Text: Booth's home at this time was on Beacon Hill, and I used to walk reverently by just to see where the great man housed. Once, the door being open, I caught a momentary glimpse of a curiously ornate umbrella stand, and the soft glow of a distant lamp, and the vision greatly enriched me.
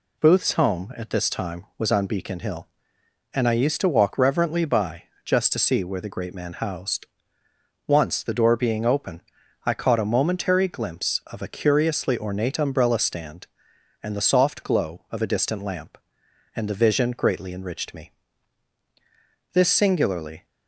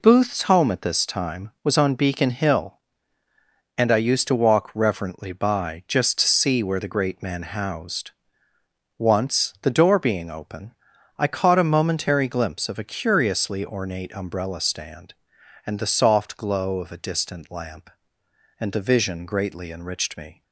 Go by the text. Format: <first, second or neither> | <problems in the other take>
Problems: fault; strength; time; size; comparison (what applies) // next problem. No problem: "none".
second | pauses between "by" and "just"; slight; at 5.0 s; 0.20 s long // goes on to say "This singularly"; noticeable; from 19.5 s on; 0.92 s long